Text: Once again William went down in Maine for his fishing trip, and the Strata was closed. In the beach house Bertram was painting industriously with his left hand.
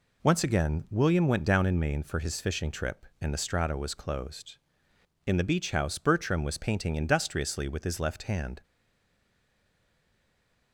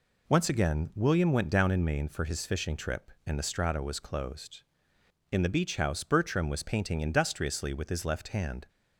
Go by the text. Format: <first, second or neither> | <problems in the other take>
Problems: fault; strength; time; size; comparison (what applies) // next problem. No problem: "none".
second | stays silent after the last word; from 8.6 s on; 2.1 s long